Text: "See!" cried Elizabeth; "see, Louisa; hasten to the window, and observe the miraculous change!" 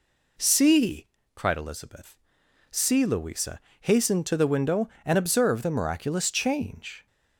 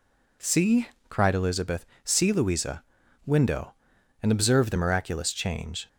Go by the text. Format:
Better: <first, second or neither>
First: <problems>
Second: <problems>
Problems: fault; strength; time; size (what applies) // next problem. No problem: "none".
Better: first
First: none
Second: skips "hasten to the"; at 3.0 s